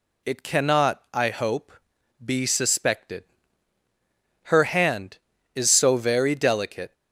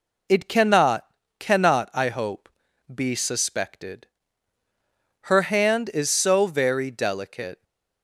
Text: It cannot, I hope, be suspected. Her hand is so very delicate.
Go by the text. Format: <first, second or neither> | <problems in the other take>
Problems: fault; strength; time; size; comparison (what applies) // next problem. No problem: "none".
first | says "cannot" twice; at 1.3 s